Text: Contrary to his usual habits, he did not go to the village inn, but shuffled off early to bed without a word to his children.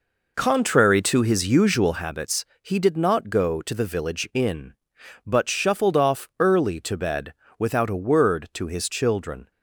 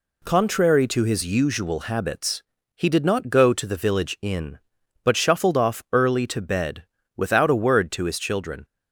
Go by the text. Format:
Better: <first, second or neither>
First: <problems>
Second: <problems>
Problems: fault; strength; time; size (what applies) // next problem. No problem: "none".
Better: second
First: starts louder than the rest; noticeable; until 2.1 s; 4.5 dB // pauses between "bed" and "without"; slight; at 7.3 s; 0.26 s long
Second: pauses between "bed" and "without"; slight; at 6.8 s; 0.32 s long